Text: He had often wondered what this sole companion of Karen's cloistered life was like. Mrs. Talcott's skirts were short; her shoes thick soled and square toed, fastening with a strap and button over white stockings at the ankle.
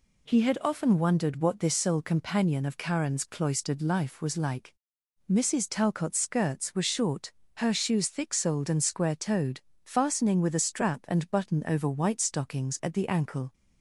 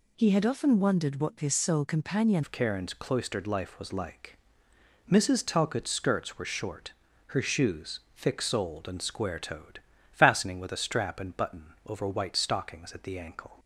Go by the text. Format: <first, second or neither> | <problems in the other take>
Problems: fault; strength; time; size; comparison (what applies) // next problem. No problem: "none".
first | changes voice at "of"; from 2.4 s on; 11.1 s long // pauses between "shoes" and "thick"; slight; at 8.0 s; 0.16 s long